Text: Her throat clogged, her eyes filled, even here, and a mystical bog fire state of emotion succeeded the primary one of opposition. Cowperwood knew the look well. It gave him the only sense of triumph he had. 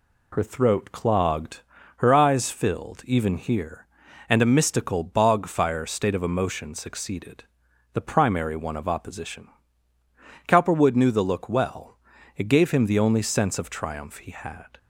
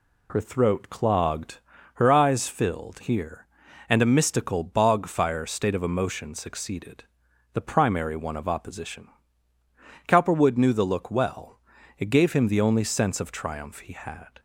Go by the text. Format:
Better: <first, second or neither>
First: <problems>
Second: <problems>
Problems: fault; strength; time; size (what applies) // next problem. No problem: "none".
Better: first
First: pauses between "succeeded" and "the"; noticeable; at 7.4 s; 0.50 s long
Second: skips "even"; at 3.0 s // pauses between "succeeded" and "the"; noticeable; at 7.0 s; 0.50 s long